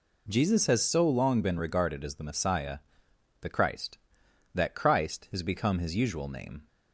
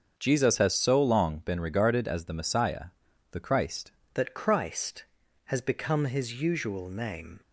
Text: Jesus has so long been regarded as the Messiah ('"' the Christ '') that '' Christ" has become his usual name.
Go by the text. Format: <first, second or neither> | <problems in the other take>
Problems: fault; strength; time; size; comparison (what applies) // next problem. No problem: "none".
first | starts louder than the rest; until 1.1 s; 6 dB // changes voice at "that"; from 4.1 s on; 3.3 s long